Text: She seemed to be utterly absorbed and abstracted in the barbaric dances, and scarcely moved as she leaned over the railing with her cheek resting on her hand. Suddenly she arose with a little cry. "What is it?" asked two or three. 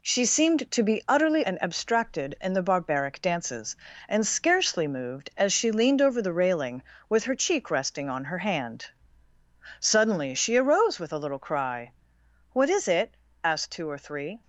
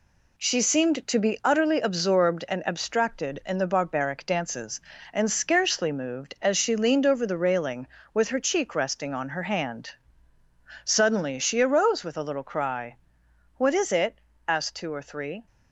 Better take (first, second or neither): second